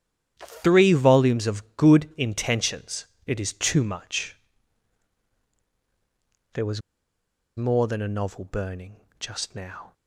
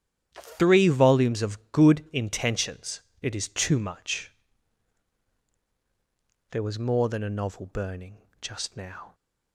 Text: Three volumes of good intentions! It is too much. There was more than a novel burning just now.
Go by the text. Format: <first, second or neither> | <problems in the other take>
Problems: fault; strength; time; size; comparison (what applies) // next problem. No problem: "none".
second | starts louder than the rest; strong; until 1.3 s; 10 dB; strong in the second // pauses between "was" and "more"; noticeable; at 6.8 s; 0.75 s long // pauses between "burning" and "just"; slight; at 8.9 s; 0.22 s long; slight in the second